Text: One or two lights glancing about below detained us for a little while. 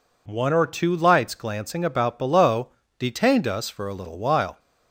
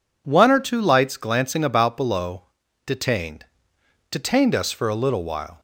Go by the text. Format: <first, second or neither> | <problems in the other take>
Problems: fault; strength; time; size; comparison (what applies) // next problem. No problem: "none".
first | pauses between "below" and "detained"; at 2.4 s; 0.42 s long; slight in the first // says "detained" twice; at 4.0 s